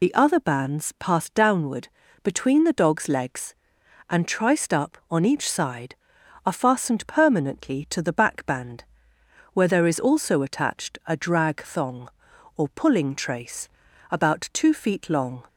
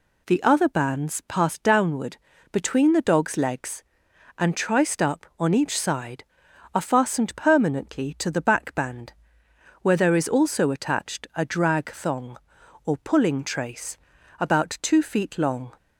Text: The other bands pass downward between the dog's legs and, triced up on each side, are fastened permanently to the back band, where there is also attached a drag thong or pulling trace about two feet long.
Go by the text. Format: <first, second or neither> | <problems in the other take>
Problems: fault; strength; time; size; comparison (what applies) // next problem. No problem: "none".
second | loses the start of "The"; at 0.0 s; 45 ms // pauses between "downward" and "between"; slight; at 1.8 s; 0.36 s long; slight in the second // pauses between "trace" and "about"; at 13.6 s; 0.42 s long; also in the second